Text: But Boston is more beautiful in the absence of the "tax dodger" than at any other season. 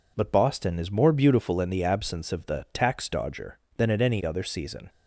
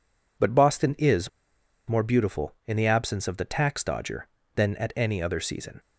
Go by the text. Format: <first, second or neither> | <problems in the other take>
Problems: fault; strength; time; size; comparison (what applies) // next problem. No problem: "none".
first | pauses between "is" and "more"; noticeable; at 1.2 s; 0.60 s long